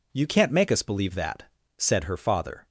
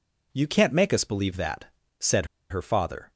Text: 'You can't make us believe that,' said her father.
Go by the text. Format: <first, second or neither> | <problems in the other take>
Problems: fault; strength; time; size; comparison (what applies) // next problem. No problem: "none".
first | pauses between "said" and "her"; slight; at 2.2 s; 0.24 s long